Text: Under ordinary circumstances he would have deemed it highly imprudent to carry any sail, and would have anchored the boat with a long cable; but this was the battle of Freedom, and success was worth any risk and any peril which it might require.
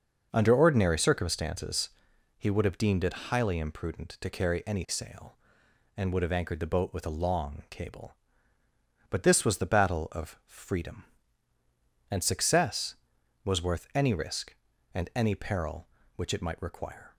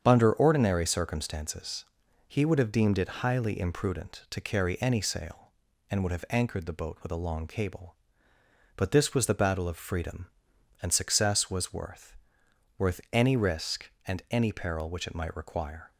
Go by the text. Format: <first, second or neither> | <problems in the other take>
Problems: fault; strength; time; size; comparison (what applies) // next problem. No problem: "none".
first | starts louder than the rest; strong; until 1.0 s; 7.5 dB; also in the first // pauses between "circumstances" and "he"; at 1.8 s; 0.42 s long; noticeable in the first // says "worth" twice; at 12.7 s